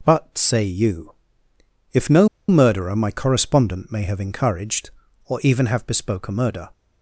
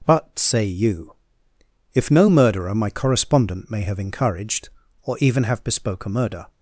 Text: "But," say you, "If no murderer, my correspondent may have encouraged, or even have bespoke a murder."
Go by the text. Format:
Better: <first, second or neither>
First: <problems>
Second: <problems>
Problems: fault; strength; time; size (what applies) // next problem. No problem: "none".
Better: second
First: pauses between "no" and "murderer"; slight; at 2.2 s; 0.20 s long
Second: none